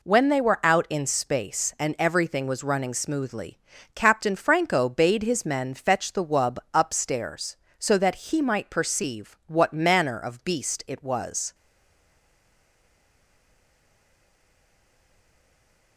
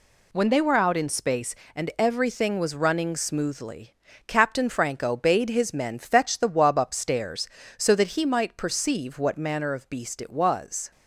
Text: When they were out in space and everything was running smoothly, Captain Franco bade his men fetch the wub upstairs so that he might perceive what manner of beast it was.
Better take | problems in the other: second | pauses between "wub" and "upstairs"; slight; at 6.5 s; 0.16 s long // stays silent after the last word; strong; from 11.5 s on; 4.4 s long

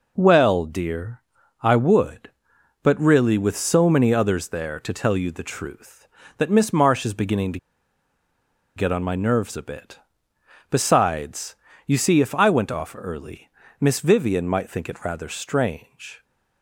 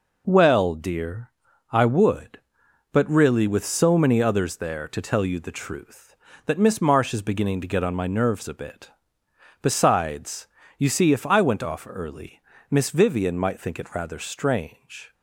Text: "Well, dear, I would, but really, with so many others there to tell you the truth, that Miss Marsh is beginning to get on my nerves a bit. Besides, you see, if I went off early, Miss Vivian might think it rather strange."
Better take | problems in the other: second | pauses between "to" and "get"; at 7.5 s; 1.1 s long

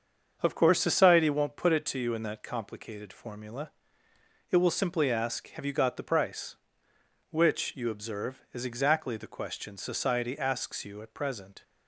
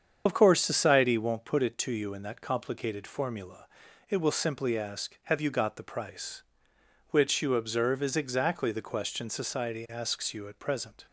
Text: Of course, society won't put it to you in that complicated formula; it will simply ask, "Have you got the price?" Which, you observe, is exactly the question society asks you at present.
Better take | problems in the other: first | loses the start of "Of"; at 0.2 s; 55 ms // starts louder than the rest; strong; until 1.2 s; 7.5 dB; also in the first

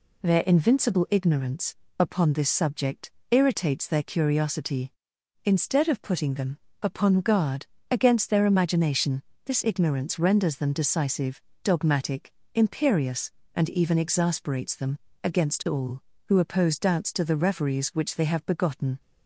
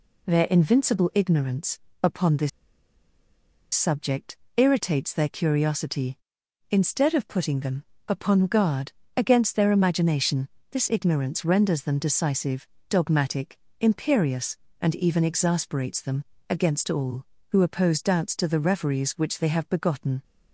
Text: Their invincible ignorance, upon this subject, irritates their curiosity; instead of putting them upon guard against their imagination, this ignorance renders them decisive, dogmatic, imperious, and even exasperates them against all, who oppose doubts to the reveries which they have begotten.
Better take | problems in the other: first | pauses between "this" and "subject"; strong; at 2.4 s; 1.2 s long // pauses between "them" and "upon"; slight; at 7.8 s; 0.24 s long; slight in the first // pauses between "guard" and "against"; slight; at 8.9 s; 0.24 s long; slight in the first // pauses between "them" and "against"; slight; at 16.2 s; 0.24 s long; slight in the first

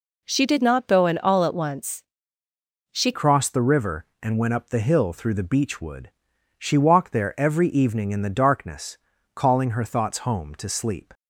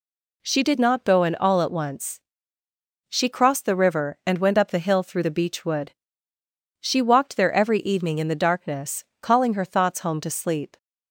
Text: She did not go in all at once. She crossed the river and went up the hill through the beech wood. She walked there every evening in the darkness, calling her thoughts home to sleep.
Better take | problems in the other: second | changes voice at "crossed"; from 3.1 s on; 8.0 s long

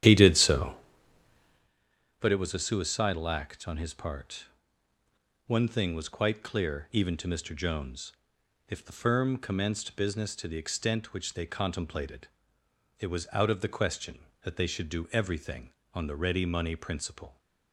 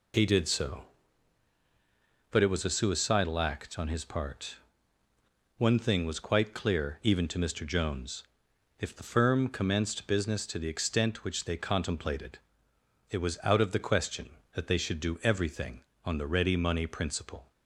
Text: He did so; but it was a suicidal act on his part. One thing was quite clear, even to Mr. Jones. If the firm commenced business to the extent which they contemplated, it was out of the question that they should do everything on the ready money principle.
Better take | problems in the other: second | starts louder than the rest; strong; until 1.7 s; 10.5 dB

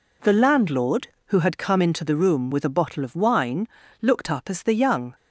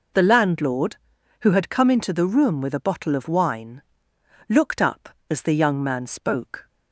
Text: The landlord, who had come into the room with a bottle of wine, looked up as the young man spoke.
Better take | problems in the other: second | stops before "man spoke"; at 5.1 s

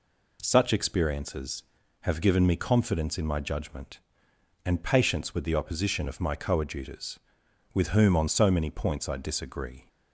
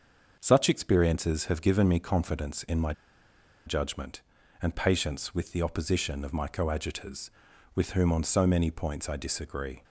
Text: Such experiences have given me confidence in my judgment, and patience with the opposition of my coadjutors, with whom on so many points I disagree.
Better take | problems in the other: first | starts louder than the rest; until 1.4 s; 6.5 dB // pauses between "my" and "judgment"; noticeable; at 2.9 s; 0.74 s long

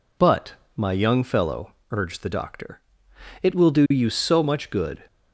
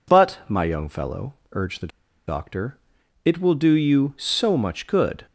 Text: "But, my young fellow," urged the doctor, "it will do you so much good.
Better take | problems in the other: first | pauses between "the" and "doctor"; at 1.9 s; 0.39 s long

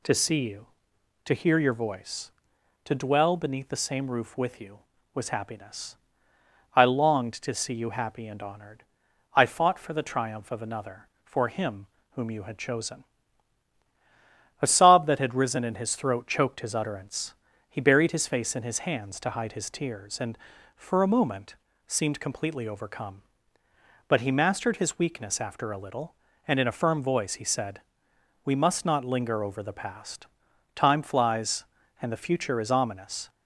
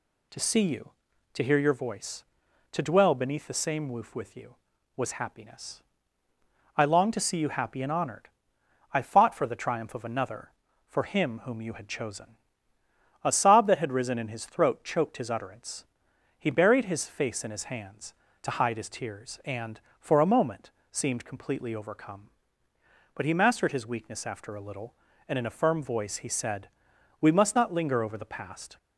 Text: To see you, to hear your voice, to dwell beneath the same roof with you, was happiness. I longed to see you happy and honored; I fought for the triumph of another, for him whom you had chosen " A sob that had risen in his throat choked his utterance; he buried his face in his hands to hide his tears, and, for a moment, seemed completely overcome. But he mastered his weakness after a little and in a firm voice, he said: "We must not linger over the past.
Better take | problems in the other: second | pauses between "him" and "whom"; slight; at 11.8 s; 0.28 s long // goes on to say "Time flies and the future is ominous"; strong; from 30.7 s on; 2.5 s long

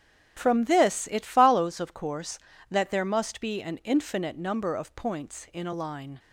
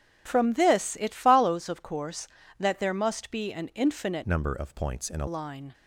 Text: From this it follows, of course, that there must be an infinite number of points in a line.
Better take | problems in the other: first | starts louder than the rest; strong; until 1.2 s; 9.5 dB; strong in the first // changes voice from "number" to "a"; from 4.2 to 5.2 s; 1.0 s long

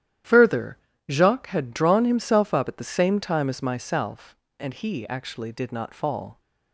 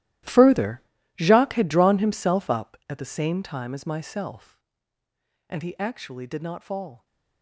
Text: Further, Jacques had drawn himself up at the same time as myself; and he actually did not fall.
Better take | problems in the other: first | gets quieter; strong; throughout; 17.5 dB // starts louder than the rest; strong; until 1.6 s; 14.5 dB; strong in the first

